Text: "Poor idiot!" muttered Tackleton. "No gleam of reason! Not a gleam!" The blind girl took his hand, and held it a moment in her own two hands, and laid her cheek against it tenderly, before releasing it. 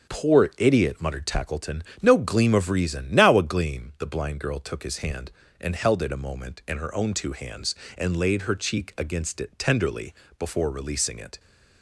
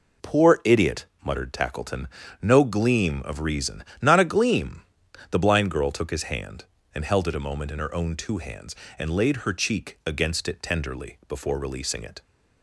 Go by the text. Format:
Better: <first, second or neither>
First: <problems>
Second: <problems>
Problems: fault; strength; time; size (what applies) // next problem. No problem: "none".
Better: second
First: starts louder than the rest; until 1.1 s; 7 dB // says "Now" for "Not"; at 3.1 s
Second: none